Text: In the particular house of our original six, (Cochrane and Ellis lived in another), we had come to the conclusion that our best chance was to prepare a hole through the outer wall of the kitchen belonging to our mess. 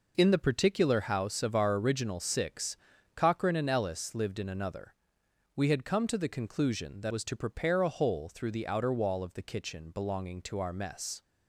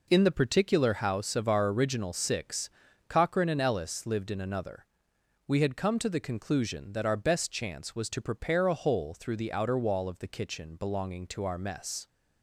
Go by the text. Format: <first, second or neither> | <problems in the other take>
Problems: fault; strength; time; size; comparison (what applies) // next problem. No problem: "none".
second | skips "our best chance"; at 7.1 s